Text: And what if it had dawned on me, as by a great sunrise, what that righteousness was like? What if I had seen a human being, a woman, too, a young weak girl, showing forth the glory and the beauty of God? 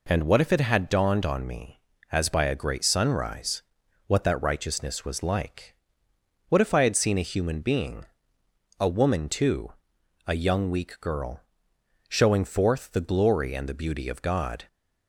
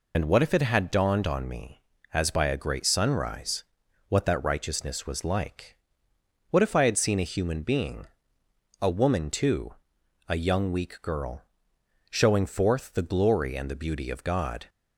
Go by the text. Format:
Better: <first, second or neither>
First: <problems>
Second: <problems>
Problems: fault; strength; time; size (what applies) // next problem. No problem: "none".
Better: first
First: none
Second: loses the start of "And"; at 0.1 s; 70 ms